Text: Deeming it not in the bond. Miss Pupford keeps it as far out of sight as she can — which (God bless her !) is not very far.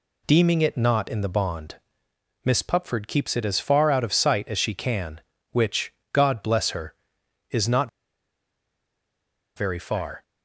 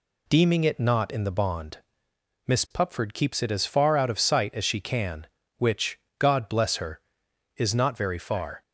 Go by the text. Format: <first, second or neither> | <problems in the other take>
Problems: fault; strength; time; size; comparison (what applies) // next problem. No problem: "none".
second | pauses between "not" and "very"; strong; at 7.8 s; 1.6 s long